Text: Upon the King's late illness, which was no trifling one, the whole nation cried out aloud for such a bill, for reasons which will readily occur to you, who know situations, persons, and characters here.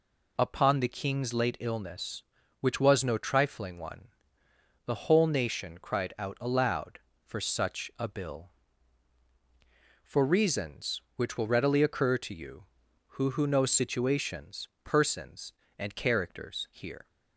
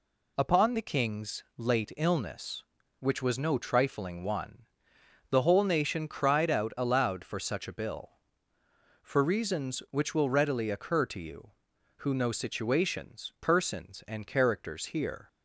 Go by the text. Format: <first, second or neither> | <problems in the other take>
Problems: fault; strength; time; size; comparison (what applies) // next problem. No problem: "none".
second | says "who" twice; at 13.3 s